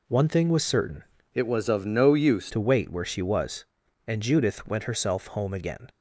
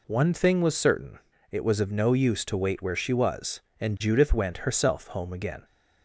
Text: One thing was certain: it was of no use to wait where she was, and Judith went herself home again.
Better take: second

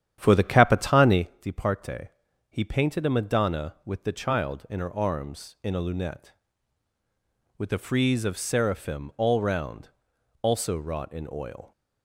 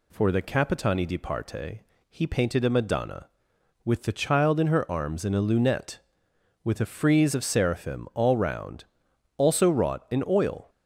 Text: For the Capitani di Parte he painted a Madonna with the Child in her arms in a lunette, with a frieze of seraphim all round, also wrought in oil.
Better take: second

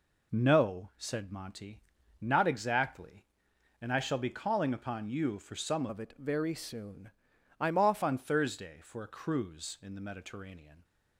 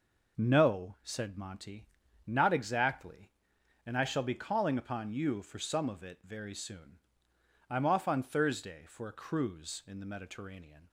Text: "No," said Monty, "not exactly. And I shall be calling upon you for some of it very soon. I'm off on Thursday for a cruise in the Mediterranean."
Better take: second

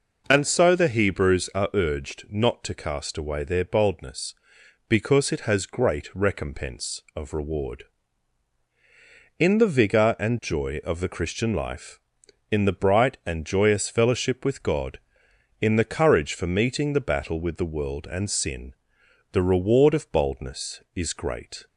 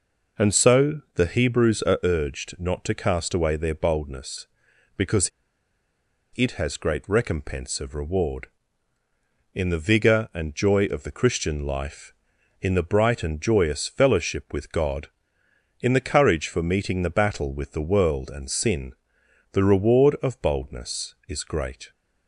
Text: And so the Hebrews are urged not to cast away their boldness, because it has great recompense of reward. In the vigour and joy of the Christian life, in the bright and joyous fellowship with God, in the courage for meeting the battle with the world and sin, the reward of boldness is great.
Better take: first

